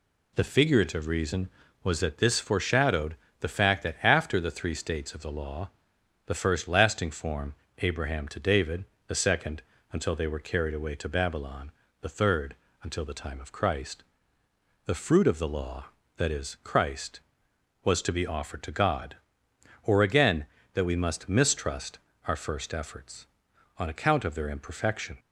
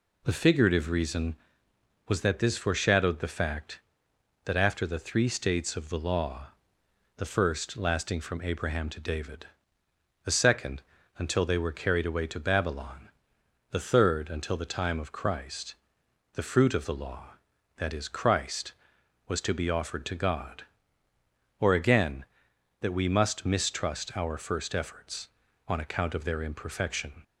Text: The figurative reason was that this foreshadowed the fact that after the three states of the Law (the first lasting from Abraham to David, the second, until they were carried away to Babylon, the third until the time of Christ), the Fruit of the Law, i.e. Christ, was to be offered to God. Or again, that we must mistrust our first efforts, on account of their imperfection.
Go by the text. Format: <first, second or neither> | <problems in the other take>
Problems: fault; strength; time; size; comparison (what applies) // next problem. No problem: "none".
second | pauses between "foreshadowed" and "the"; slight; at 3.1 s; 0.26 s long // says "form" for "from"; at 7.1 s // pauses between "third" and "until"; slight; at 12.5 s; 0.26 s long // pauses between "mistrust" and "our"; slight; at 21.9 s; 0.28 s long